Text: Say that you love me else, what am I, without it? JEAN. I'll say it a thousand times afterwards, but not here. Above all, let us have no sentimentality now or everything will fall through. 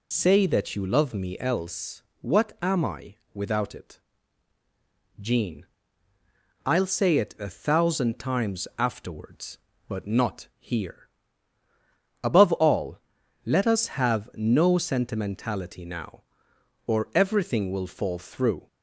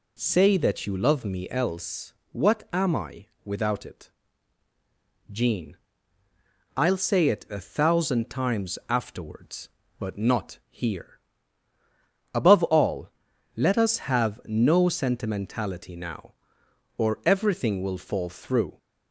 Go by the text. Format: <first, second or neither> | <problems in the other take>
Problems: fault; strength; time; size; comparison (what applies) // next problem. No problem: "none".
second | loses the start of "Say"; at 0.1 s; 30 ms